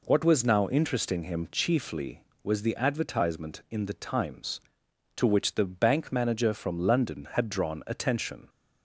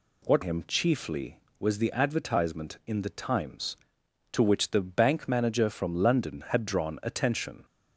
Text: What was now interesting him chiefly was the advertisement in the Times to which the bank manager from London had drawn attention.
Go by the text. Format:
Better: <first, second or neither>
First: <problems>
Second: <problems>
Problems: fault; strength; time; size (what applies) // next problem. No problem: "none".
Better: first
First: none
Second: skips "was now interesting"; at 0.4 s